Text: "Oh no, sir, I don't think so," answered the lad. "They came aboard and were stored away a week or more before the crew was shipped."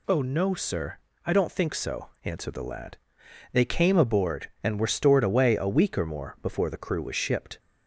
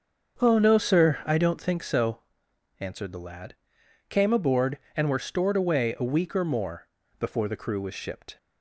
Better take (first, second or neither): first